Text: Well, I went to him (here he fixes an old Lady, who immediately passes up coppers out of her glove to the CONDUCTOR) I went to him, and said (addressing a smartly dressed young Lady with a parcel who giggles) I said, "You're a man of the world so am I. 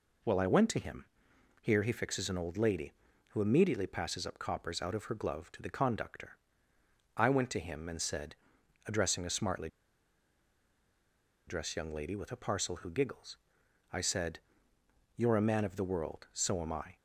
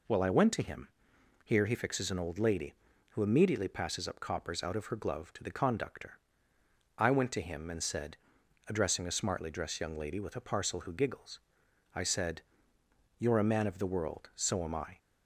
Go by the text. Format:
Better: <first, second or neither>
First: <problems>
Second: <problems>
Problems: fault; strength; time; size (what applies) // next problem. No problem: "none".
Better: second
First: pauses between "smartly" and "dressed"; strong; at 9.6 s; 1.7 s long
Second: none